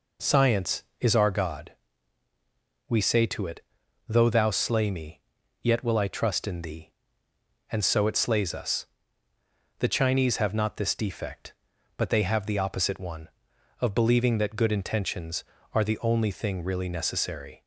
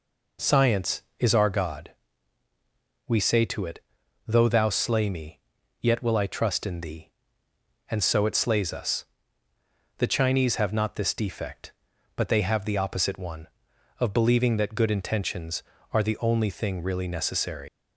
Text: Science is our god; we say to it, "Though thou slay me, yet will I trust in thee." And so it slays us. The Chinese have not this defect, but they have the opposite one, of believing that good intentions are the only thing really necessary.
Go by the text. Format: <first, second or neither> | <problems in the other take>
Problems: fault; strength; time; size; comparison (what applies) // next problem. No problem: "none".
first | leaves "necessary" unfinished; at 17.6 s; 135 ms